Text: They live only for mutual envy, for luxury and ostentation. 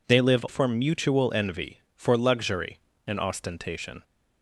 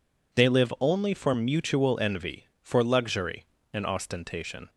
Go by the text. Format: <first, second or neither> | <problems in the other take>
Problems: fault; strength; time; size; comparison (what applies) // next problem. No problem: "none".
second | skips "only"; at 0.4 s